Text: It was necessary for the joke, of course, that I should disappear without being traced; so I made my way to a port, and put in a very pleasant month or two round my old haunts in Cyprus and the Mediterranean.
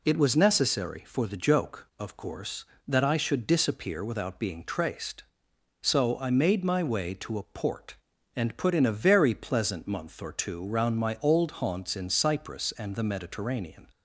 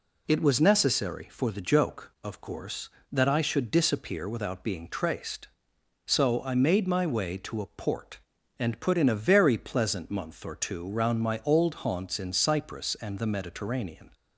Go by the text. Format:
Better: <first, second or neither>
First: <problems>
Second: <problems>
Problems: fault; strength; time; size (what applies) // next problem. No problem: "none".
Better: neither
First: none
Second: none